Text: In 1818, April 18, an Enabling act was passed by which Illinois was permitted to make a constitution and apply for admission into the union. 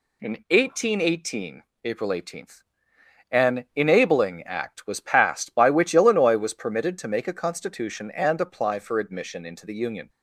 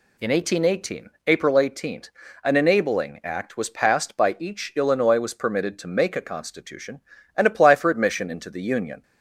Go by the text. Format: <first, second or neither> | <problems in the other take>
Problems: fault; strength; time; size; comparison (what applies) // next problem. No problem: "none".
first | says "each" for "which"; at 4.3 s